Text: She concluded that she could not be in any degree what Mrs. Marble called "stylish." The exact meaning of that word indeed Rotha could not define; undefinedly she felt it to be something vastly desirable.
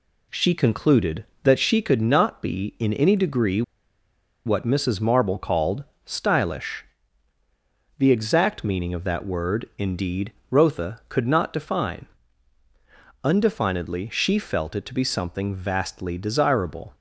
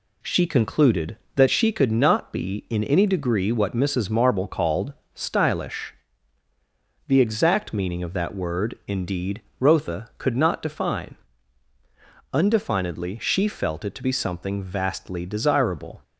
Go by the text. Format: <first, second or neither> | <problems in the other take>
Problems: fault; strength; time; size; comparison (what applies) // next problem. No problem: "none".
second | pauses between "degree" and "what"; noticeable; at 3.6 s; 0.84 s long // pauses between "called" and "stylish"; slight; at 5.8 s; 0.22 s long; slight in the second // pauses between "indeed" and "Rotha"; slight; at 10.3 s; 0.20 s long; slight in the second